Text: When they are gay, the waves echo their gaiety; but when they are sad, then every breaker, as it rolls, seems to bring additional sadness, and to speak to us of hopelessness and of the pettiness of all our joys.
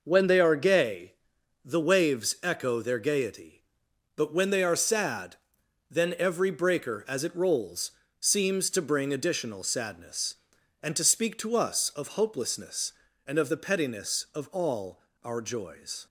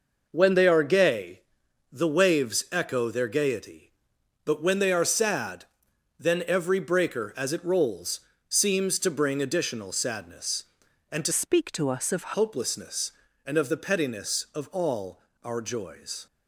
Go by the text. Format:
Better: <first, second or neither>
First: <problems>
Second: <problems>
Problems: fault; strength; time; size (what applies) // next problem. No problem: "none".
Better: first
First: pauses between "all" and "our"; slight; at 15.0 s; 0.24 s long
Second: changes voice from "speak" to "of"; from 11.3 to 12.3 s; 1.0 s long // pauses between "all" and "our"; slight; at 15.2 s; 0.24 s long